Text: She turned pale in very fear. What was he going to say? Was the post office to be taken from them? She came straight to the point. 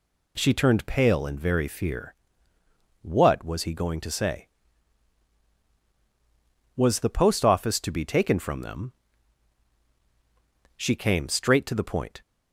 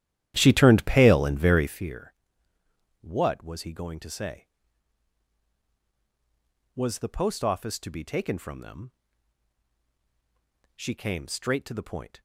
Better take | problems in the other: first | starts louder than the rest; strong; until 1.9 s; 12 dB

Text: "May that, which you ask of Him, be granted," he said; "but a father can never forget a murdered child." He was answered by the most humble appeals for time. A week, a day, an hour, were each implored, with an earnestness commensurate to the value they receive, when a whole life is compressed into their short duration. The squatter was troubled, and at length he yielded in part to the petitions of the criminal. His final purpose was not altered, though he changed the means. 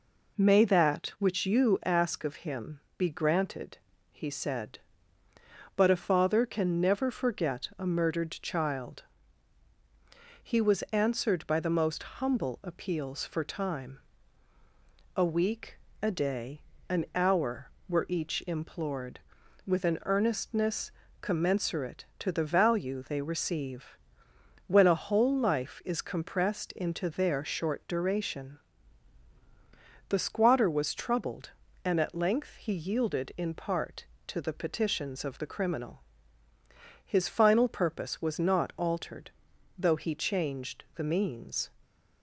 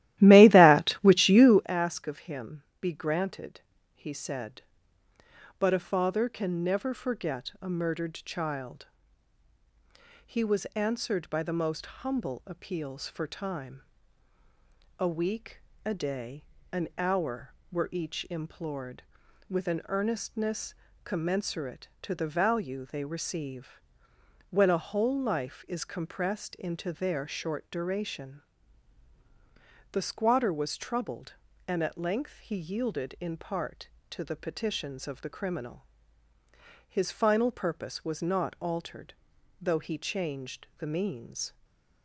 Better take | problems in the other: first | starts louder than the rest; strong; until 1.7 s; 15 dB // pauses between "earnestness" and "commensurate"; slight; at 20.7 s; 0.30 s long; slight in the first // stays silent after the last word; slight; from 41.4 s on; 0.6 s long

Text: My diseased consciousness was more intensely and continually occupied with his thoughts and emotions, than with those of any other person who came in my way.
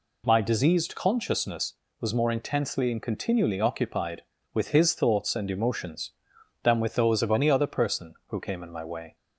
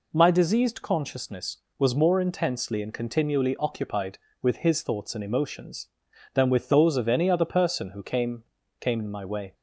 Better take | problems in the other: first | says "came" twice; at 8.7 s

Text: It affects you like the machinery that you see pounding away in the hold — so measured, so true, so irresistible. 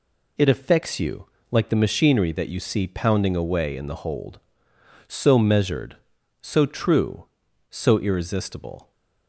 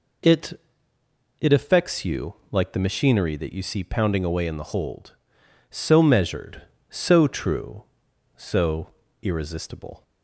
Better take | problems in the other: first | says "It" twice; at 1.3 s // pauses between "you" and "like"; slight; at 2.3 s; 0.16 s long; slight in the first // pauses between "so" and "irresistible"; slight; at 8.8 s; 0.34 s long

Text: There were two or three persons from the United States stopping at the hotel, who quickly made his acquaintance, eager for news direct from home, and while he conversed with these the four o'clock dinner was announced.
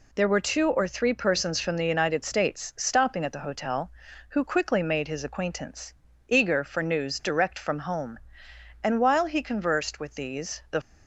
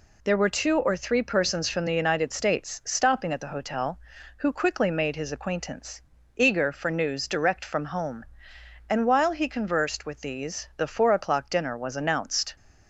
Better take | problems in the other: second | stops before "four o'clock dinner was announced"; at 10.8 s

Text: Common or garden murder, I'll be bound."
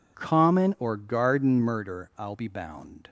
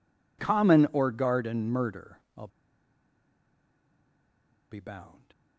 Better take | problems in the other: first | pauses between "I'll" and "be"; strong; at 2.4 s; 2.2 s long

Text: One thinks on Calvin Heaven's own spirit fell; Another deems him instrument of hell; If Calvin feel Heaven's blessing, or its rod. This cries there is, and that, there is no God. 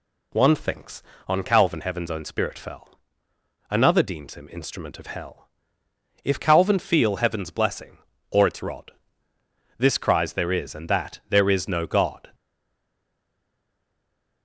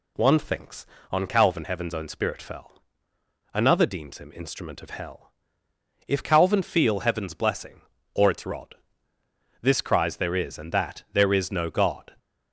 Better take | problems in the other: second | stays silent after the last word; noticeable; from 12.3 s on; 2.1 s long

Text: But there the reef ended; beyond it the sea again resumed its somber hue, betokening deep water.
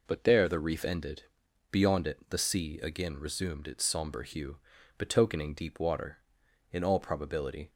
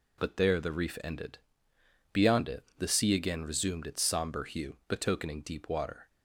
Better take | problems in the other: second | goes on to say "In all probability"; noticeable; from 6.7 s on; 0.98 s long

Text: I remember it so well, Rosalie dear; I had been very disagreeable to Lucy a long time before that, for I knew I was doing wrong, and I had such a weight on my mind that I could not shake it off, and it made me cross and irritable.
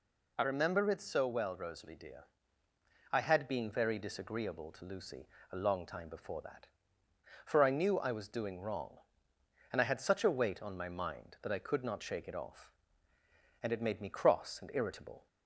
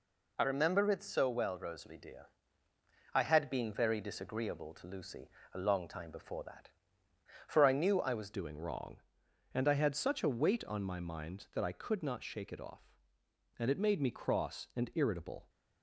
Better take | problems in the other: first | pauses between "Lucy" and "a"; slight; at 5.2 s; 0.24 s long; slight in the first // changes voice at "doing"; from 8.3 s on; 7.1 s long

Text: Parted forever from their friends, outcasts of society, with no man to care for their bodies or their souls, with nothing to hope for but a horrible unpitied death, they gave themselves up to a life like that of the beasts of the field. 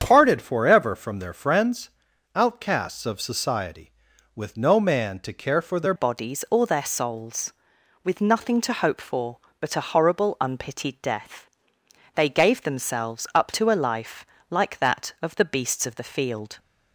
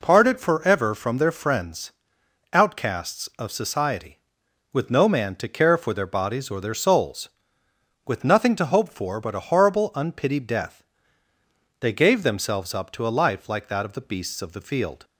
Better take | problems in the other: second | starts louder than the rest; strong; until 1.0 s; 8 dB // changes voice at "bodies"; from 5.9 s on; 10.6 s long // pauses between "life" and "like"; slight; at 14.2 s; 0.24 s long

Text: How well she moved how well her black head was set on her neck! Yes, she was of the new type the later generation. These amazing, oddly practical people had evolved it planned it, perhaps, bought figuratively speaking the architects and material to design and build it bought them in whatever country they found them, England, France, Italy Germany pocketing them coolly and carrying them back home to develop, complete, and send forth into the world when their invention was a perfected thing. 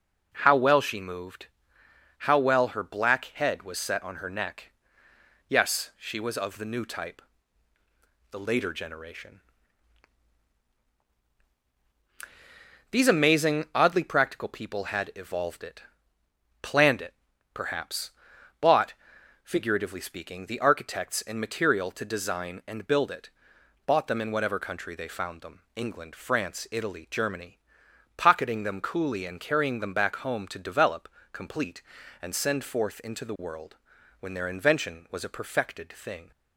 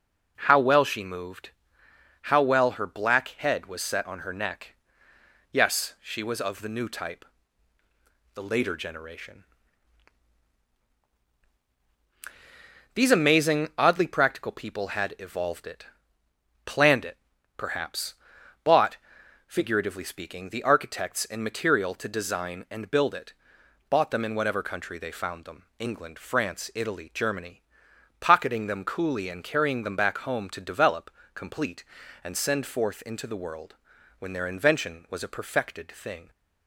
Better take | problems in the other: neither | pauses between "moved" and "how"; noticeable; the same in both // pauses between "type" and "the"; the same in both // pauses between "it" and "planned"; noticeable; the same in both // pauses between "bought" and "figuratively"; noticeable; the same in both // pauses between "it" and "bought"; noticeable; the same in both // pauses between "Germany" and "pocketing"; noticeable; the same in both // pauses between "world" and "when"; the same in both

